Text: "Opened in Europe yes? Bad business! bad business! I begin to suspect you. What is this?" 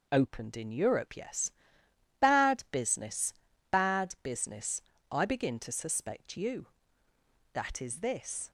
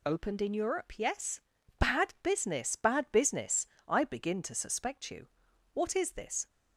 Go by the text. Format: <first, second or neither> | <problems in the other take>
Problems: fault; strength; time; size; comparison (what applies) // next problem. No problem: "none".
second | says "That" for "What"; at 7.5 s